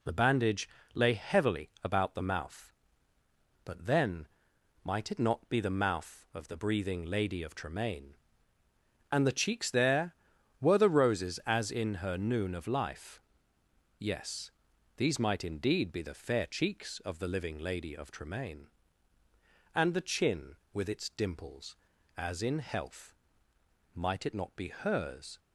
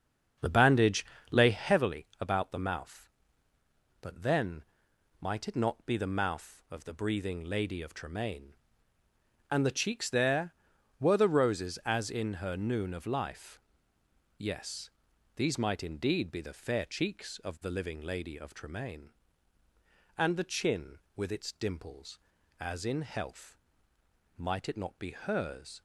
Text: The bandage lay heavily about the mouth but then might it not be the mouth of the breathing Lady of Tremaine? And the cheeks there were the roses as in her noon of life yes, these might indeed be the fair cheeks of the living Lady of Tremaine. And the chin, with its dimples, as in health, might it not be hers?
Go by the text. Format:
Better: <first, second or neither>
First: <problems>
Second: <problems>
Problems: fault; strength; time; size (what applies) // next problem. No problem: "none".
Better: first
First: pauses between "bandage" and "lay"; slight; at 0.6 s; 0.28 s long // pauses between "then" and "might"; noticeable; at 4.2 s; 0.56 s long // pauses between "life" and "yes"; noticeable; at 13.2 s; 0.78 s long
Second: starts louder than the rest; strong; until 1.8 s; 7 dB // pauses between "bandage" and "lay"; slight; at 1.0 s; 0.28 s long // pauses between "then" and "might"; noticeable; at 4.6 s; 0.56 s long // pauses between "life" and "yes"; noticeable; at 13.5 s; 0.78 s long